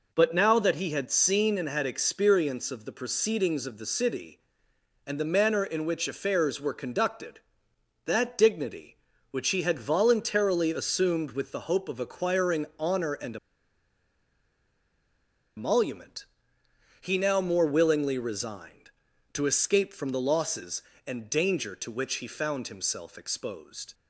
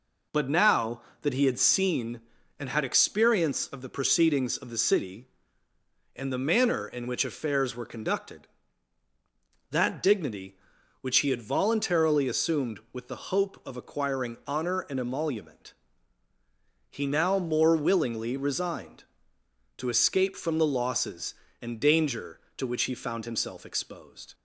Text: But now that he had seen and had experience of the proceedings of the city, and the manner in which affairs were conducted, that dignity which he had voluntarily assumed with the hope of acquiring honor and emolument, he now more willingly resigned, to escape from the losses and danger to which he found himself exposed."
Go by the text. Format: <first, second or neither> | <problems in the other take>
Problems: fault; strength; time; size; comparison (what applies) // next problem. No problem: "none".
second | pauses between "and" and "emolument"; strong; at 13.3 s; 2.2 s long